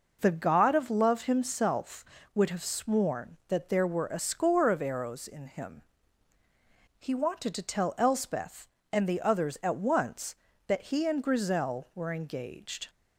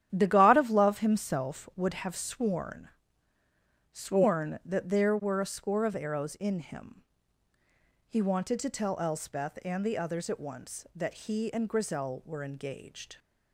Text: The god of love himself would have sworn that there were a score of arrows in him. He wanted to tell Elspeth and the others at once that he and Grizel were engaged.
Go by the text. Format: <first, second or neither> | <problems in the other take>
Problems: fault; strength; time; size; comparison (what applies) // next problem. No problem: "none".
first | starts louder than the rest; strong; until 1.1 s; 10.5 dB // says "sworn" twice; at 3.9 s